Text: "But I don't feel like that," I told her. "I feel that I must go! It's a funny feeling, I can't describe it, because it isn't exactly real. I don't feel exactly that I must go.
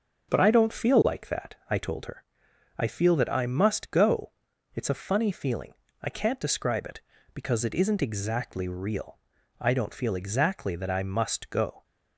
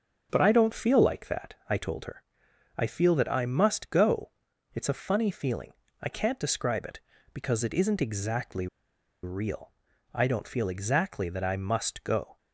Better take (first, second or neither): first